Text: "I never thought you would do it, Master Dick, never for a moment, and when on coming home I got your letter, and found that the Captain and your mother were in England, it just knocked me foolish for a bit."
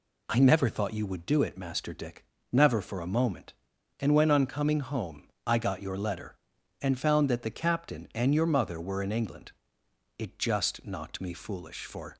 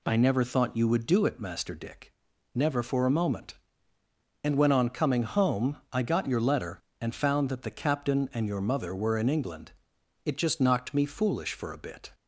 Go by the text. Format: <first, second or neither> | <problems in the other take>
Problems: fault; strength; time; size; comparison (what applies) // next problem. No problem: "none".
second | pauses between "home" and "I"; slight; at 5.2 s; 0.18 s long; slight in the second // stops before "a bit"; at 12.1 s